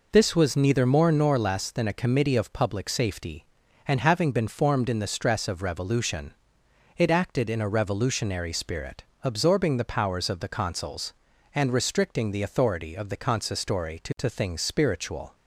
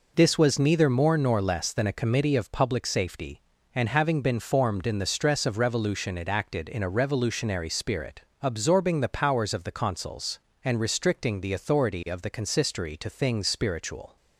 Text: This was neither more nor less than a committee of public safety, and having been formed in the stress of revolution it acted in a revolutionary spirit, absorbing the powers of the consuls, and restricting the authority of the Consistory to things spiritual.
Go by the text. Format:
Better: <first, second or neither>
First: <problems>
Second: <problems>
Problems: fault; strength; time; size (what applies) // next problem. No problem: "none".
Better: second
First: pauses between "revolution" and "it"; noticeable; at 6.3 s; 0.64 s long // says "to" twice; at 14.1 s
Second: none